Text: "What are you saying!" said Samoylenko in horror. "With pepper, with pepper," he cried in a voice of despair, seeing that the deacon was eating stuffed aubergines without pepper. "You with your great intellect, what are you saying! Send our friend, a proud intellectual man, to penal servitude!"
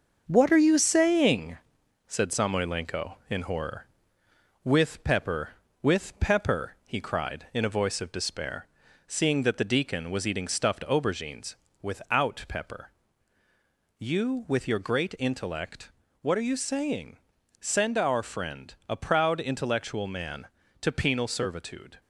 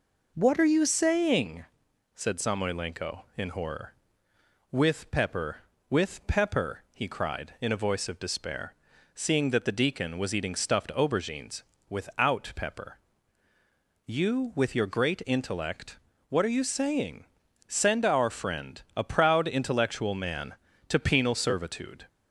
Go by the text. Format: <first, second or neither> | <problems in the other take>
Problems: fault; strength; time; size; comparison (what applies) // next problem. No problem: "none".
second | gets quieter; noticeable; throughout; 5.5 dB // pauses between "aubergines" and "without"; slight; at 11.5 s; 0.26 s long; slight in the second